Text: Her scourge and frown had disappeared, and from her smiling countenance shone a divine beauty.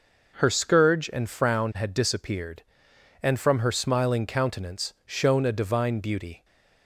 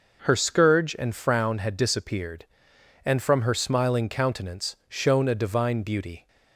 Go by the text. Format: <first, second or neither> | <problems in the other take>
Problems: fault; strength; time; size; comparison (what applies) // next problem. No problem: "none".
neither | none